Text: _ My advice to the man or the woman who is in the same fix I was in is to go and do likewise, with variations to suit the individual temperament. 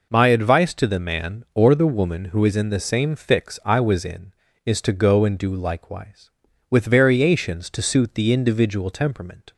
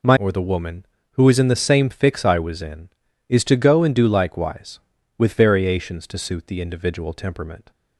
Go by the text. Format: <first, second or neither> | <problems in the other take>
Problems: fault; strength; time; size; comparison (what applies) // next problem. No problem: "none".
first | skips "advice to the man"; at 0.1 s